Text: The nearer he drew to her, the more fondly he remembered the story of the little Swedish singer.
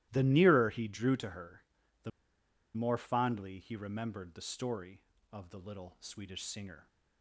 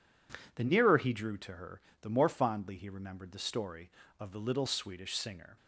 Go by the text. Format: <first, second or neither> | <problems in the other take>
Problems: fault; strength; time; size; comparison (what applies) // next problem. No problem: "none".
second | starts louder than the rest; strong; until 1.1 s; 15.5 dB // pauses between "the" and "more"; noticeable; at 2.1 s; 0.64 s long